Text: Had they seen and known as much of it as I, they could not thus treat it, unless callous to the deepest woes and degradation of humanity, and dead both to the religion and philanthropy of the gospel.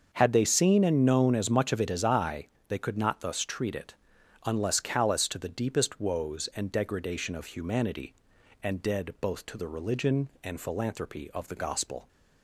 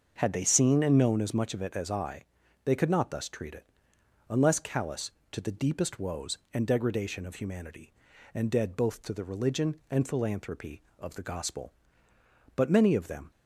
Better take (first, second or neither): first